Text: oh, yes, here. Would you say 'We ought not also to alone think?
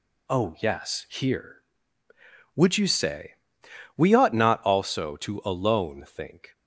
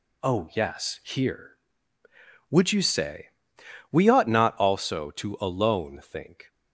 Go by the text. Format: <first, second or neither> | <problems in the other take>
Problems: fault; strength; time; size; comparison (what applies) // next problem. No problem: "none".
neither | pauses between "say" and "We"; noticeable; the same in both